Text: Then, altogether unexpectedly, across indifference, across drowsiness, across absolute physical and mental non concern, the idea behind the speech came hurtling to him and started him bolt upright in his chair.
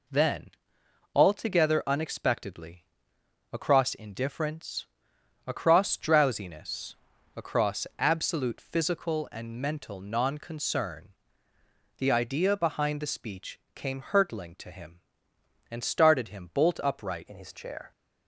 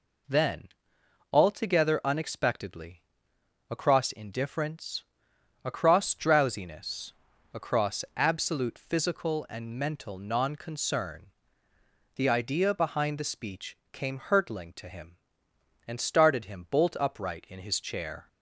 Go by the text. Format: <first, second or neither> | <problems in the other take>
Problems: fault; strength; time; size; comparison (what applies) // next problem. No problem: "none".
second | pauses between "speech" and "came"; slight; at 13.5 s; 0.16 s long; slight in the second // changes voice at "in"; from 17.2 s on; 0.7 s long